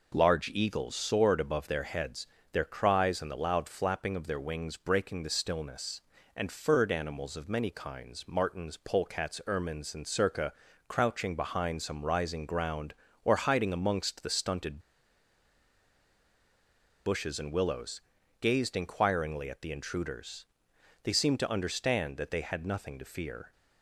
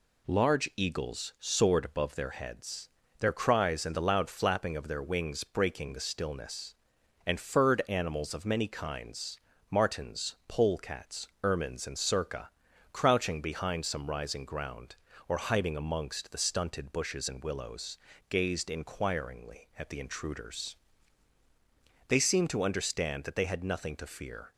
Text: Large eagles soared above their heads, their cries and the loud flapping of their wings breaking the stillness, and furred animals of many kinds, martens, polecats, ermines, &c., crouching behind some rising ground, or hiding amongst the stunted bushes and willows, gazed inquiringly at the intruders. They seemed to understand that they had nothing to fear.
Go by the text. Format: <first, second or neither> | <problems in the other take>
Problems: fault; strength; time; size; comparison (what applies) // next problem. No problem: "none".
second | pauses between "stunted" and "bushes"; strong; at 14.7 s; 2.2 s long